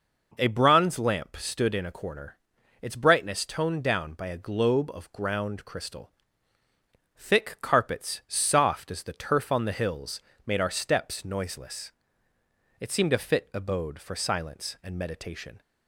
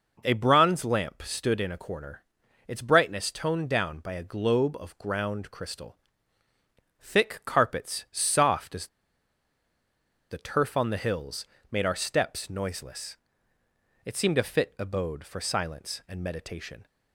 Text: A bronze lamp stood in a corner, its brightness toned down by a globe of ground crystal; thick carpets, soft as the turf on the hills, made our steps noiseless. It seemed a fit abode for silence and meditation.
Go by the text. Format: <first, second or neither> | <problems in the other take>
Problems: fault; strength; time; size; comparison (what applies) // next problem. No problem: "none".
first | pauses between "as" and "the"; strong; at 8.8 s; 1.4 s long